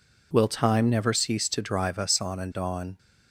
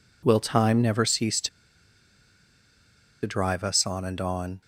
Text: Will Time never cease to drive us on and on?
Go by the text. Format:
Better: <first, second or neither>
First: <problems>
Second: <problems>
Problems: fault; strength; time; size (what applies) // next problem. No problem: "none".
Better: first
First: none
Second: pauses between "to" and "drive"; strong; at 1.4 s; 1.7 s long